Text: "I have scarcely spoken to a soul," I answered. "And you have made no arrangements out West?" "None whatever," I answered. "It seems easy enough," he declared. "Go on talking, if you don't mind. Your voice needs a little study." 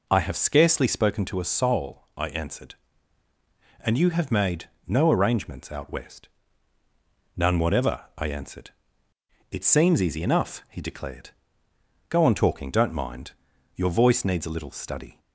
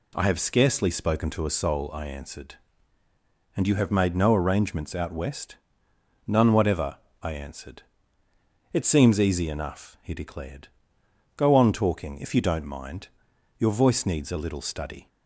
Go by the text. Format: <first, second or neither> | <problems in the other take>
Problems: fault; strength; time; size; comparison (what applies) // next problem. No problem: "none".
second | pauses between "made" and "no"; slight; at 4.6 s; 0.16 s long // skips "if you"; at 12.6 s